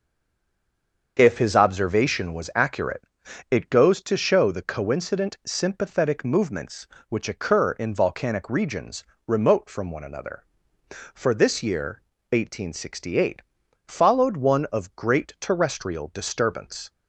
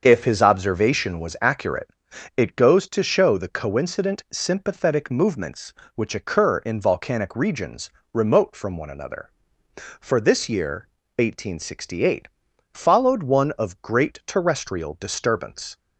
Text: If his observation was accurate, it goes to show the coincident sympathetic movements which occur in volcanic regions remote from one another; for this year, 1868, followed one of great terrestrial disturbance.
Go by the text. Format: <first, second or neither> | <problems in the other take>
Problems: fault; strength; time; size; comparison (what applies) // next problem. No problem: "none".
second | stays silent before the first word; until 1.1 s; 1.1 s long // starts louder than the rest; until 2.2 s; 6.5 dB; also in the second // pauses between "regions" and "remote"; slight; at 9.0 s; 0.22 s long; slight in the second